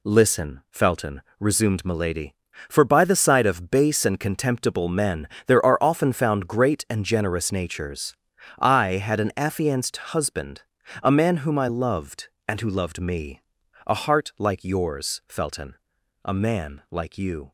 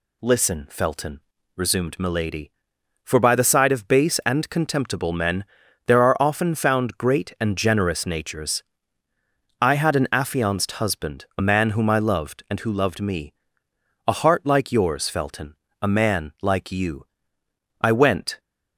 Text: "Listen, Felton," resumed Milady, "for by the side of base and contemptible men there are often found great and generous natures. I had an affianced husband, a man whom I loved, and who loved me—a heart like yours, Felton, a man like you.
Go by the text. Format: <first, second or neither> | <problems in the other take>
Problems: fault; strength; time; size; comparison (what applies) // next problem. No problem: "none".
first | pauses between "men" and "there"; at 5.4 s; 0.44 s long; slight in the first // goes on to say "I went"; from 17.8 s on; 0.58 s long